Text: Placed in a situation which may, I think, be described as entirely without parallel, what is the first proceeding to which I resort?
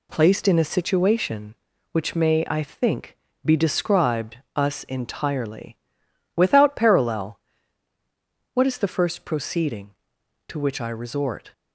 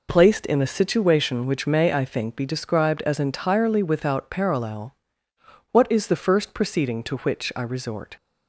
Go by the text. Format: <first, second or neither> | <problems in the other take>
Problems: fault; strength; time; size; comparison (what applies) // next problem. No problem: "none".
second | says "us" for "as"; at 4.5 s // pauses between "entirely" and "without"; noticeable; at 5.7 s; 0.58 s long